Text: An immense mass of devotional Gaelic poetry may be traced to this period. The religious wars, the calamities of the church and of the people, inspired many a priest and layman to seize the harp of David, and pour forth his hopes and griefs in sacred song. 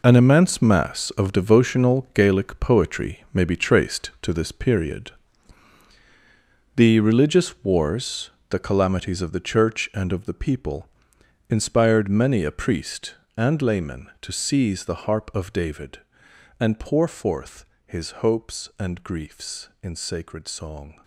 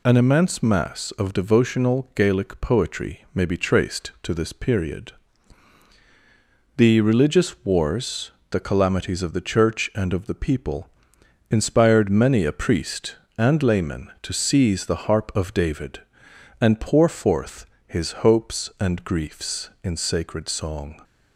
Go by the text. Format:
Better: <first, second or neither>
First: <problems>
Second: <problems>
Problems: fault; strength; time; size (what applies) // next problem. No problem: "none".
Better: second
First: gets quieter; strong; throughout; 11.5 dB // pauses between "forth" and "his"; slight; at 17.6 s; 0.20 s long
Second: pauses between "forth" and "his"; slight; at 17.6 s; 0.20 s long